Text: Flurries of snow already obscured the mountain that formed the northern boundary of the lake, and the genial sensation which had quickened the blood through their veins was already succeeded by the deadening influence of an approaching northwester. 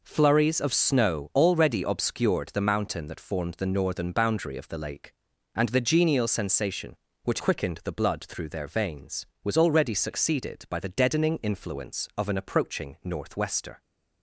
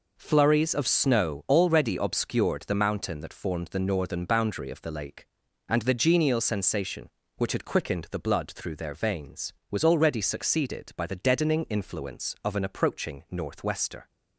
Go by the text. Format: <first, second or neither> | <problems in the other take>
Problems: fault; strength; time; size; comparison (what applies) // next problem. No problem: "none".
second | skips "had"; at 7.3 s